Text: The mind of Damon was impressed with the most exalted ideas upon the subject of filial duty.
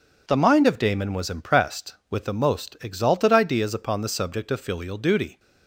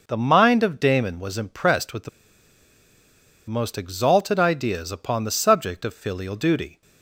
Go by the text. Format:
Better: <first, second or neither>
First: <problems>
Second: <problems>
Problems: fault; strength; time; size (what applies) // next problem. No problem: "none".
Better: first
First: none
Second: pauses between "the" and "most"; strong; at 2.0 s; 1.3 s long